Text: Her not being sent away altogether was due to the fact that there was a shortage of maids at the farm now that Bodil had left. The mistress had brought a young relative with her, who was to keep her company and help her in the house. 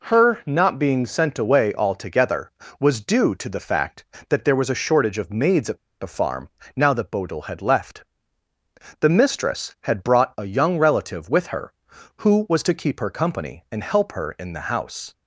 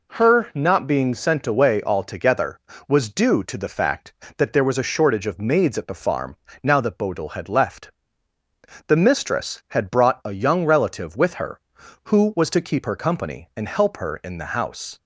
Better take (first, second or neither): second